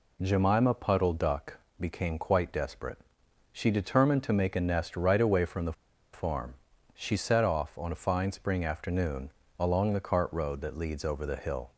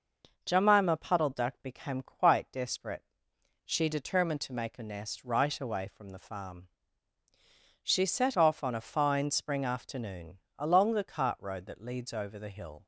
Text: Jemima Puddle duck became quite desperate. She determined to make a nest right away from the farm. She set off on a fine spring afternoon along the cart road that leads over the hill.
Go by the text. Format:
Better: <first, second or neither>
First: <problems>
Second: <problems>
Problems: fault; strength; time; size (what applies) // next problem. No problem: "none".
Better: second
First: pauses between "duck" and "became"; slight; at 1.5 s; 0.20 s long // pauses between "the" and "farm"; at 5.7 s; 0.40 s long // pauses between "afternoon" and "along"; slight; at 9.2 s; 0.30 s long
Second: pauses between "afternoon" and "along"; slight; at 10.3 s; 0.18 s long